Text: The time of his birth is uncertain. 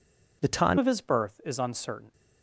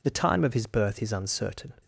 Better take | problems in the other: second | changes voice at "of"; from 0.7 s on; 1.4 s long

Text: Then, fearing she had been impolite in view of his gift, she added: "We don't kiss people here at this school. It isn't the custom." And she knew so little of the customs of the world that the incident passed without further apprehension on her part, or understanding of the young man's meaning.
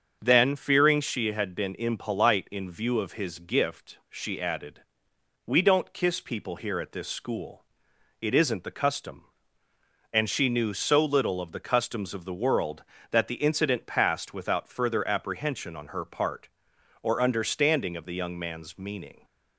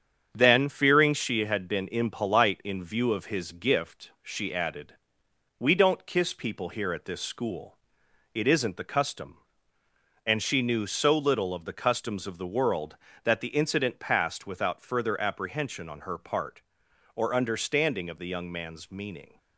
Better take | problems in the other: first | gets quieter; noticeable; throughout; 5 dB // starts louder than the rest; strong; until 1.3 s; 7.5 dB; also in the first

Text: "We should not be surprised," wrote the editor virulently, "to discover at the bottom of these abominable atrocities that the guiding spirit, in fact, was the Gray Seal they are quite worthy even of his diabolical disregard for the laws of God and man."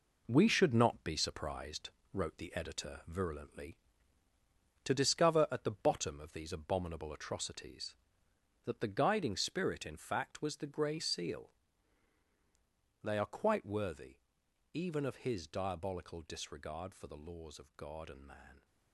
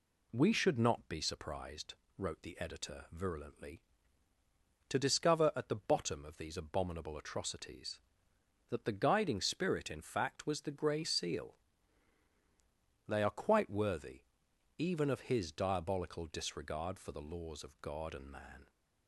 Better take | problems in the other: second | gets quieter; throughout; 7 dB // pauses between "Seal" and "they"; strong; at 11.5 s; 1.5 s long; strong in the second // pauses between "worthy" and "even"; noticeable; at 14.1 s; 0.56 s long; noticeable in the second

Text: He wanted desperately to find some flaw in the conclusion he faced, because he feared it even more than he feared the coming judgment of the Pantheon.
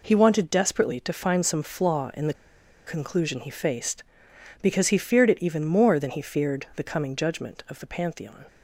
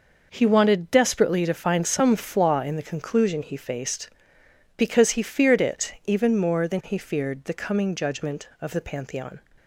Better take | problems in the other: second | pauses between "the" and "conclusion"; noticeable; at 2.3 s; 0.52 s long

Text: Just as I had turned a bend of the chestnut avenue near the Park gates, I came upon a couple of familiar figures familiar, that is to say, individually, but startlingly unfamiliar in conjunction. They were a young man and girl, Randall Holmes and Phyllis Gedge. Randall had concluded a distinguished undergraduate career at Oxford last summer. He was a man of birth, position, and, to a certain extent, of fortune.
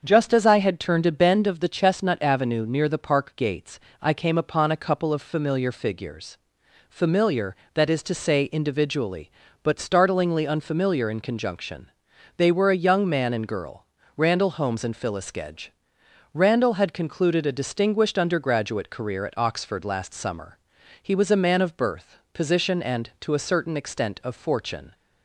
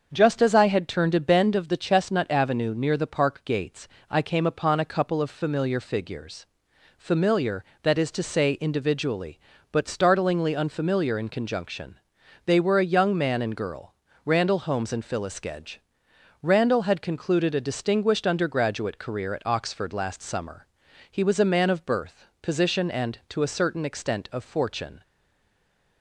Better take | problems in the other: first | starts louder than the rest; until 1.1 s; 6.5 dB; also in the first // pauses between "figures" and "familiar"; noticeable; at 6.4 s; 0.50 s long; noticeable in the first // stays silent after the last word; from 25.0 s on; 1.0 s long

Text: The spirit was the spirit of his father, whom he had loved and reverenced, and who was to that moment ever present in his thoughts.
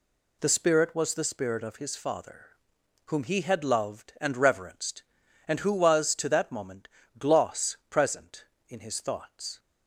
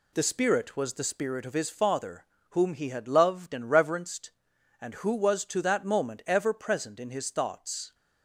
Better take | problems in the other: second | says "gloss" for "ever"; at 7.1 s

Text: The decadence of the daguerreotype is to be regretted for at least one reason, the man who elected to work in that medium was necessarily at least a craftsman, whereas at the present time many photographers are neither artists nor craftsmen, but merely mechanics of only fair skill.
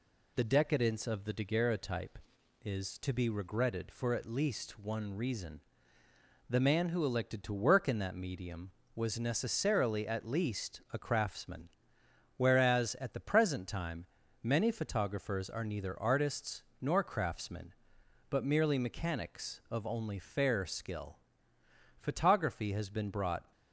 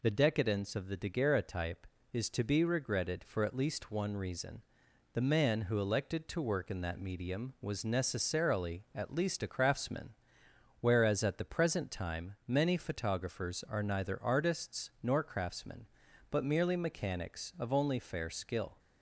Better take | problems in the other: second | pauses between "time" and "many"; slight; at 14.0 s; 0.36 s long // pauses between "artists" and "nor"; slight; at 16.6 s; 0.18 s long // goes on to say "Photography has been brought"; from 21.9 s on; 1.5 s long

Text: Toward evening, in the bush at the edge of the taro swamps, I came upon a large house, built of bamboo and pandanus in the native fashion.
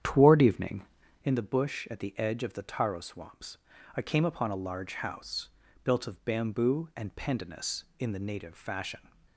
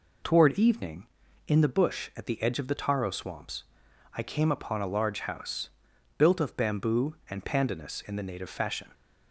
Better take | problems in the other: second | starts louder than the rest; strong; until 1.3 s; 9.5 dB

